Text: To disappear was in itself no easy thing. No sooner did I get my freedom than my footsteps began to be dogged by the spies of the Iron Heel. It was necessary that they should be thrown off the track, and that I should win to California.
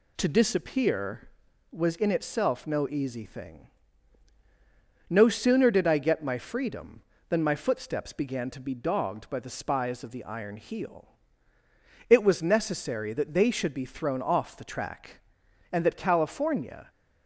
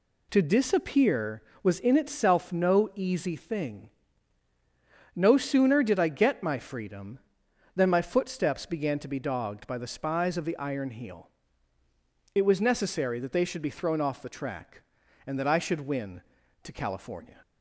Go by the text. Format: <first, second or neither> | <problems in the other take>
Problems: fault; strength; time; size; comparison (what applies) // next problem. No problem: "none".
second | skips "I should win to"; at 15.9 s